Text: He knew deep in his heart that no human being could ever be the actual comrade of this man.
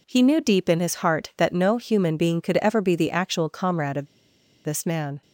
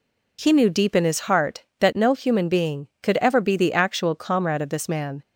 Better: second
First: pauses between "of" and "this"; noticeable; at 4.0 s; 0.58 s long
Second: none

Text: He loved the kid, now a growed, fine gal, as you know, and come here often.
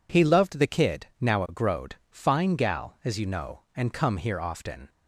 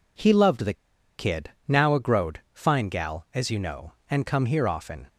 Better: first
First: none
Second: pauses between "the" and "kid"; at 0.7 s; 0.43 s long

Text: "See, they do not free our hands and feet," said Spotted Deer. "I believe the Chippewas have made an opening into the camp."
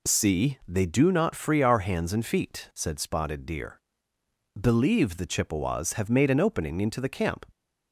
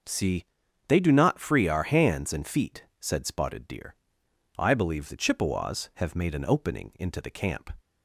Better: second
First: skips "I"; at 4.1 s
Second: none

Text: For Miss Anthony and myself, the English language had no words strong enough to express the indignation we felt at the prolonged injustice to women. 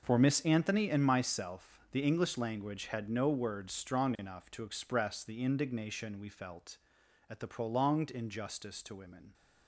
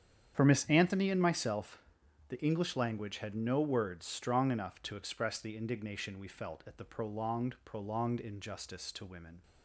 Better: first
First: none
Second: starts louder than the rest; strong; until 1.3 s; 8.5 dB // says "prolonged" twice; at 7.6 s

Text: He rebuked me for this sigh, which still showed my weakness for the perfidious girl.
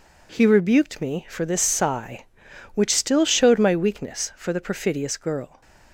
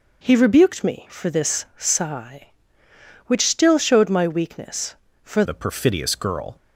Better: first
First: none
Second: changes voice at "the"; from 5.4 s on; 1.1 s long

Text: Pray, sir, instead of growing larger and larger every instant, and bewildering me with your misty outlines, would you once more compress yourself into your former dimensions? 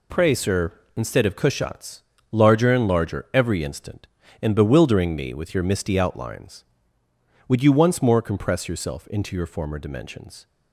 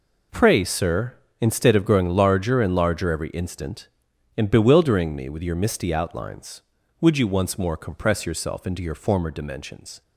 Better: second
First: says "cushats" for "growing"; at 1.3 s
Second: none

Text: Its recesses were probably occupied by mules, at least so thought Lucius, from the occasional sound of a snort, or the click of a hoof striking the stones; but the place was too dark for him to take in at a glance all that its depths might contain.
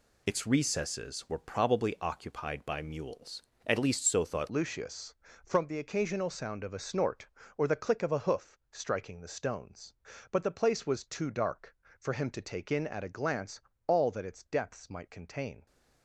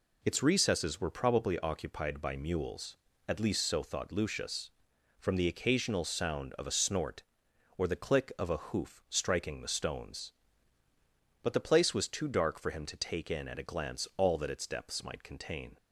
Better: second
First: changes voice at "Lucius"; from 4.4 s on; 11.2 s long // pauses between "glance" and "all"; slight; at 13.5 s; 0.28 s long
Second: none

